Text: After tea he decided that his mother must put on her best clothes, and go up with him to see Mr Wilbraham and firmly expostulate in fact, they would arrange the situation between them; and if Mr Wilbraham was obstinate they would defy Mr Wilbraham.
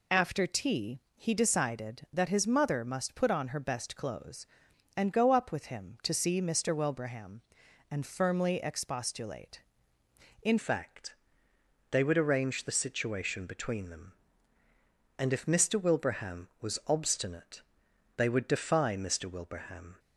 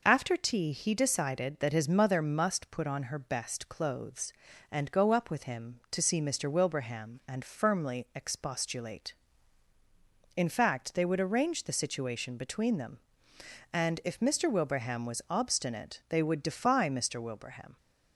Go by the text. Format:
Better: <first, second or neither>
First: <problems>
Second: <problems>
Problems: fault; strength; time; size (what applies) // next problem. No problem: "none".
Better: second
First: pauses between "tea" and "he"; slight; at 1.0 s; 0.16 s long // changes voice at "fact"; from 10.5 s on; 9.4 s long // pauses between "obstinate" and "they"; noticeable; at 17.6 s; 0.56 s long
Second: none